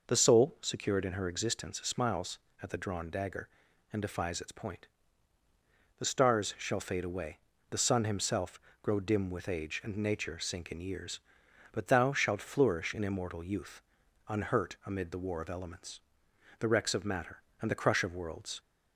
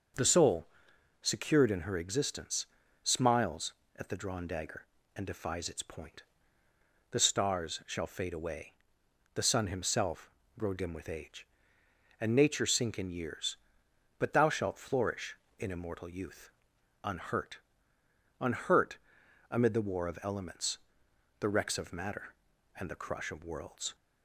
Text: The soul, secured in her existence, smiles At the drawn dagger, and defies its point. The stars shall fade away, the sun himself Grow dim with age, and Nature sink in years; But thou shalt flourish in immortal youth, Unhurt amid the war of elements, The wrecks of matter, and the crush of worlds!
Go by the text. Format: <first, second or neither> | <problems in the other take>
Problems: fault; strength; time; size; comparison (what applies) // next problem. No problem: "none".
first | starts louder than the rest; until 1.7 s; 6.5 dB // pauses between "himself" and "Grow"; slight; at 10.3 s; 0.26 s long; slight in the first // says "Unhurt" twice; at 18.3 s